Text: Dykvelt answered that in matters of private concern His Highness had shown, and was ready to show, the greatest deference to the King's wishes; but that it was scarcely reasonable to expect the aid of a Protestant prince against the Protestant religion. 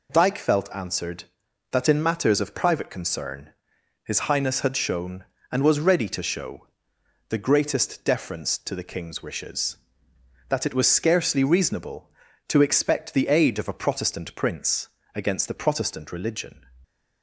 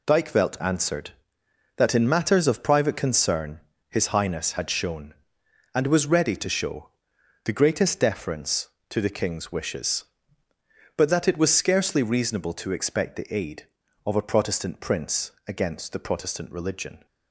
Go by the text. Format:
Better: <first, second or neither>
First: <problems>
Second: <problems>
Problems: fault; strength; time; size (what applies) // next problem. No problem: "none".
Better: second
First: pauses between "concern" and "His"; noticeable; at 3.5 s; 0.50 s long // skips "but"; at 10.1 s // pauses between "prince" and "against"; slight; at 14.8 s; 0.26 s long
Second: pauses between "concern" and "His"; slight; at 3.6 s; 0.26 s long // pauses between "prince" and "against"; slight; at 15.3 s; 0.16 s long